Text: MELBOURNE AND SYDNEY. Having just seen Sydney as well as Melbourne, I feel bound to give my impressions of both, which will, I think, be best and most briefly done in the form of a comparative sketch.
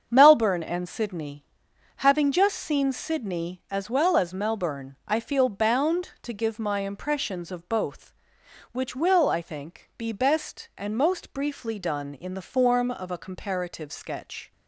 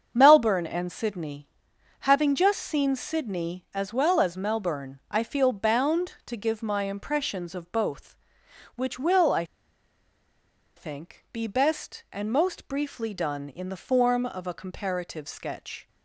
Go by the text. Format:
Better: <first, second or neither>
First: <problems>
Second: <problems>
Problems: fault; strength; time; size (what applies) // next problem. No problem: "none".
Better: first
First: starts louder than the rest; until 1.1 s; 7 dB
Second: starts louder than the rest; until 1.1 s; 7 dB // pauses between "I" and "think"; strong; at 9.4 s; 1.3 s long